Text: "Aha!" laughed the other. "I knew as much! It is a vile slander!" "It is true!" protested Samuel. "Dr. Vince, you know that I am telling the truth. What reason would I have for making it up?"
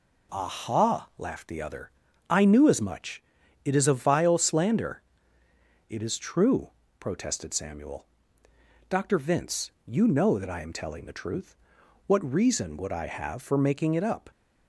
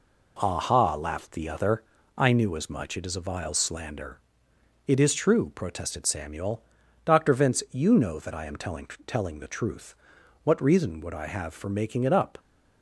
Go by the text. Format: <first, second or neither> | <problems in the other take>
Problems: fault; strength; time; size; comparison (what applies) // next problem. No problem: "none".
first | says "telling" twice; at 9.0 s